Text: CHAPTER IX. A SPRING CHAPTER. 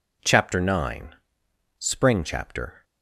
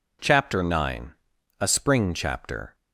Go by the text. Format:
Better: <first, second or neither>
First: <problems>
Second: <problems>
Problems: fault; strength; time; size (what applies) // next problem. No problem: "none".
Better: second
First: skips "A"; at 1.4 s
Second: none